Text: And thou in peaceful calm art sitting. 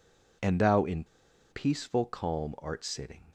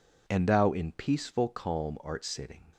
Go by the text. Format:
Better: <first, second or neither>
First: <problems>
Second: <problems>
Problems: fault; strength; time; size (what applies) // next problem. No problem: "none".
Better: second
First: pauses between "in" and "peaceful"; noticeable; at 1.0 s; 0.46 s long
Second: none